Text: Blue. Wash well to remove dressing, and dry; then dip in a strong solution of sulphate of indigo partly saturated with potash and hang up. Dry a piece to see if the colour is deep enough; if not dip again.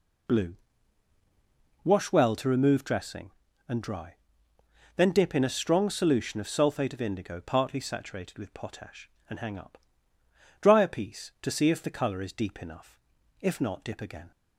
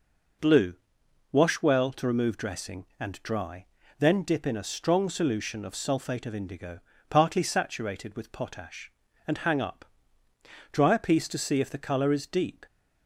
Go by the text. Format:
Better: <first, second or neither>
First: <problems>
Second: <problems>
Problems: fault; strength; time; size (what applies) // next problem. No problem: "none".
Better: first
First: none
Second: pauses between "indigo" and "partly"; slight; at 6.7 s; 0.30 s long // stops before "enough if not dip again"; at 12.6 s